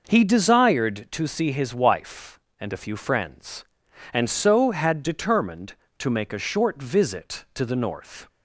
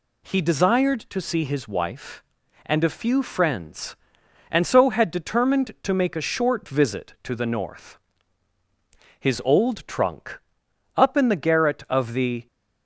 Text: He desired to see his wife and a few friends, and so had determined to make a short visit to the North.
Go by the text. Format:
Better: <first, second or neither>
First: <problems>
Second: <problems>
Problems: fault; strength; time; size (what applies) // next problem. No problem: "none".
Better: first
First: none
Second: goes on to say "His old trunk up in the garret of the"; strong; from 9.1 s on; 3.2 s long